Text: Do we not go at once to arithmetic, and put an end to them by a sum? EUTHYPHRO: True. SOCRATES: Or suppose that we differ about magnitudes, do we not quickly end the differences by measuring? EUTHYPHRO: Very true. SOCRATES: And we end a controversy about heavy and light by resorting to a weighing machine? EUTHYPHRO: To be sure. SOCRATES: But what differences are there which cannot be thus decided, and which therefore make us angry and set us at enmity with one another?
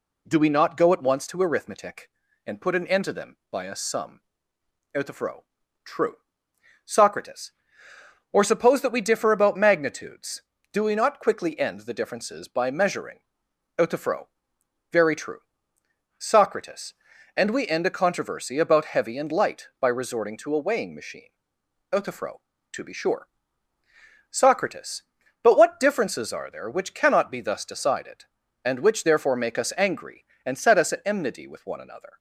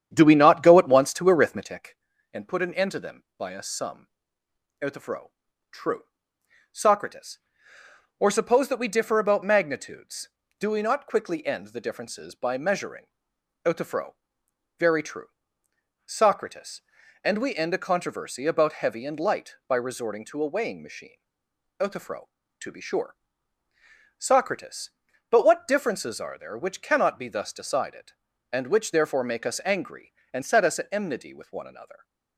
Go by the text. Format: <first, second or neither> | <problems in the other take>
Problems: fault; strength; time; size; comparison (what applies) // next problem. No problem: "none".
first | starts louder than the rest; strong; until 1.8 s; 9 dB